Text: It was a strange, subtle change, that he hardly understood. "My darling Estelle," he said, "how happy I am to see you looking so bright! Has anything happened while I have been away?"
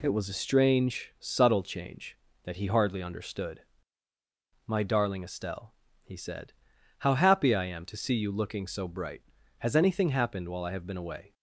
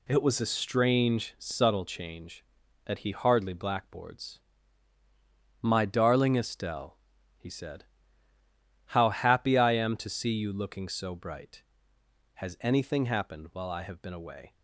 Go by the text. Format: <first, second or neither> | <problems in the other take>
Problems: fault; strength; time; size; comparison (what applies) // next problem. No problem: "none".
first | says "blackboards" for "understood"; at 3.5 s